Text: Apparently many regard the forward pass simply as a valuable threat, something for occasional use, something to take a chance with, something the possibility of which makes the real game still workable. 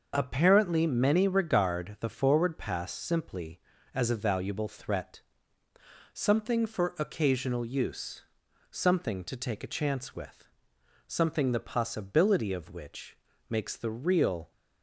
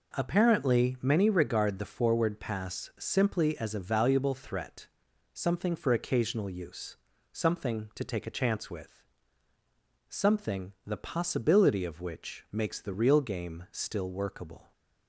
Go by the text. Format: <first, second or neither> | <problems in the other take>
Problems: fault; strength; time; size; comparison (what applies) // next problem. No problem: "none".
second | starts louder than the rest; noticeable; until 1.1 s; 6 dB // pauses between "which" and "makes"; slight; at 13.1 s; 0.32 s long // stops before "game still workable"; at 14.5 s